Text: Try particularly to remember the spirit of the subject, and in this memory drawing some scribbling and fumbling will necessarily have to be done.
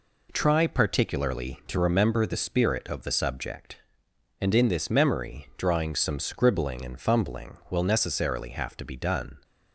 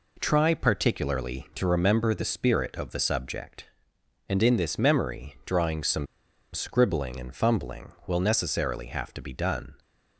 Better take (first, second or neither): first